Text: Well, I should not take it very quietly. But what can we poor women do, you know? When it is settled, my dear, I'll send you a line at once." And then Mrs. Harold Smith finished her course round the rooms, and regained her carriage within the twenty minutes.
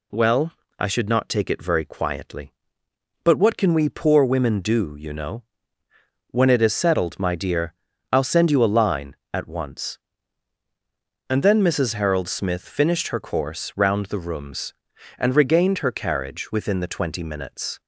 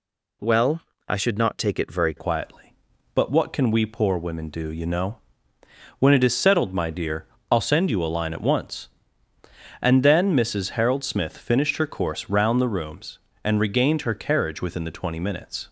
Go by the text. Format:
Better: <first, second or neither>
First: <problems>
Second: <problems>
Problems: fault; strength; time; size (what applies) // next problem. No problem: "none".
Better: first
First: none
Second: changes voice at "quietly"; from 2.1 s on; 13.5 s long